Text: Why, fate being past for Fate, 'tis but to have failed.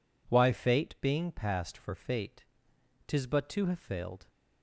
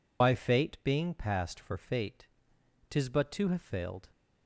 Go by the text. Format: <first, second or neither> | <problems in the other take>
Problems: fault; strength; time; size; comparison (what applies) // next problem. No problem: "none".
first | loses the start of "Why"; at 0.2 s; 110 ms